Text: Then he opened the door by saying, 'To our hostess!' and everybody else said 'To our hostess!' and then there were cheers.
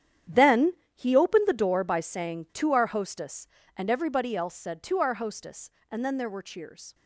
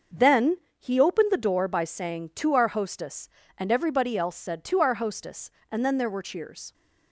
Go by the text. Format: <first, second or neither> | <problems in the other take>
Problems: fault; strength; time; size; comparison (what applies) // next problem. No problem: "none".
second | gets quieter; strong; throughout; 13 dB // starts louder than the rest; strong; until 1.4 s; 9.5 dB; noticeable in the second // pauses between "Then" and "he"; slight; at 0.7 s; 0.20 s long; slight in the second